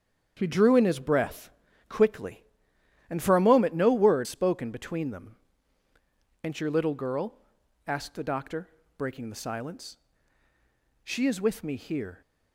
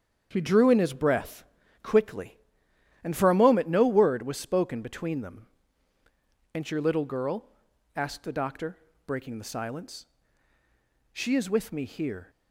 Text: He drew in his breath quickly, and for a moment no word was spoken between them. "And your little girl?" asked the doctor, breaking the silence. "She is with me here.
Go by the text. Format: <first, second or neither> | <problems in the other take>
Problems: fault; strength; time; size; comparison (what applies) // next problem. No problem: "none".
second | starts louder than the rest; strong; until 1.4 s; 8 dB; strong in the second // pauses between "breath" and "quickly"; at 1.4 s; 0.38 s long; also in the second // skips "was"; at 4.2 s